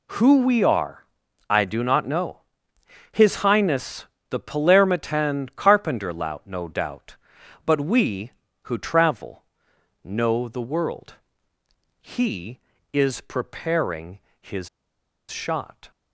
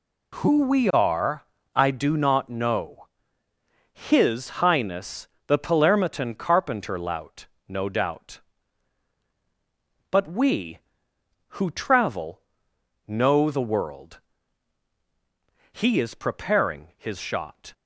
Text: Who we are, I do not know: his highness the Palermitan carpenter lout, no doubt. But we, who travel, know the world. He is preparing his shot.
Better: second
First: pauses between "highness" and "the"; slight; at 4.0 s; 0.24 s long // pauses between "preparing" and "his"; slight; at 14.2 s; 0.20 s long // pauses between "his" and "shot"; noticeable; at 14.6 s; 0.61 s long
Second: pauses between "highness" and "the"; slight; at 5.2 s; 0.18 s long

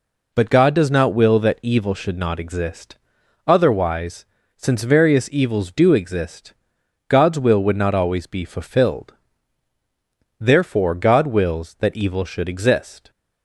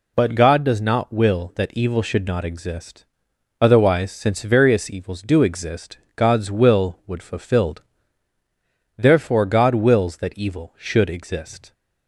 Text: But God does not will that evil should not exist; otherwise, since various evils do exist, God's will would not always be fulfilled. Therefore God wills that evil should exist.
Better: first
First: none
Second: skips "not always be"; at 7.2 s

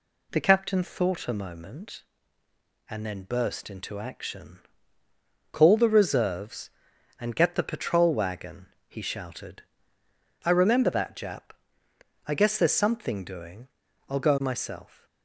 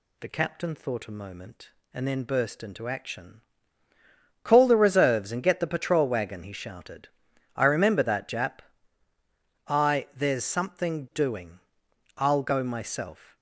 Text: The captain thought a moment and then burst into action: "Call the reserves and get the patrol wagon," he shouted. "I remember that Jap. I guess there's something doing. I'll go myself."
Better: first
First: none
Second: skips "guess"; at 10.1 s

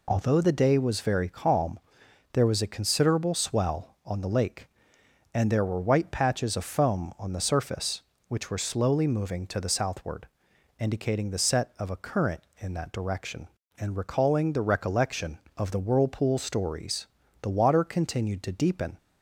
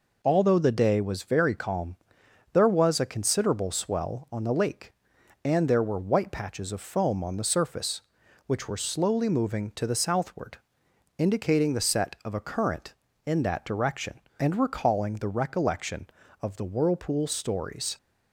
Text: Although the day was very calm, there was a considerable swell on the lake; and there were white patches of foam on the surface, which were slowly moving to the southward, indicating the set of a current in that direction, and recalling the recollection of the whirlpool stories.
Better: second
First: goes on to say "The water continued to deepen"; from 17.4 s on; 1.5 s long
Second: none

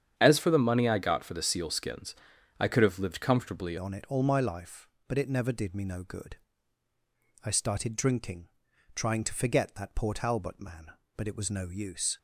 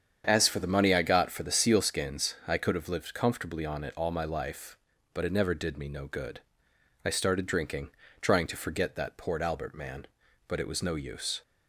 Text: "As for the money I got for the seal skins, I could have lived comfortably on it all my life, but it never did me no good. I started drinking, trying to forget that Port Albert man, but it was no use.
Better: second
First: starts louder than the rest; strong; until 1.2 s; 8.5 dB // changes voice at "on"; from 3.7 s on; 8.4 s long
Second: starts louder than the rest; strong; until 1.2 s; 8 dB

